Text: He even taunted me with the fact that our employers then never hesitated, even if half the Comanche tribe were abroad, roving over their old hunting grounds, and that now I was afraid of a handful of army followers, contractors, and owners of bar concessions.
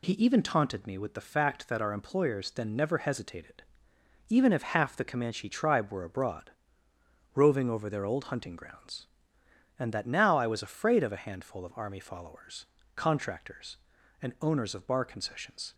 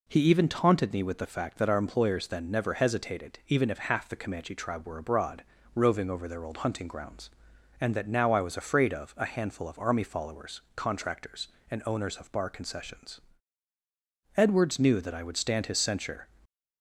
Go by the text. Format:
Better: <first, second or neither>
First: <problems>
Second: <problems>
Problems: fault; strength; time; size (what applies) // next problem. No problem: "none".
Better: first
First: none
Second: goes on to say "Edwards knew that I would stand his censure"; strong; from 14.3 s on; 1.9 s long // stays silent after the last word; slight; from 16.2 s on; 0.6 s long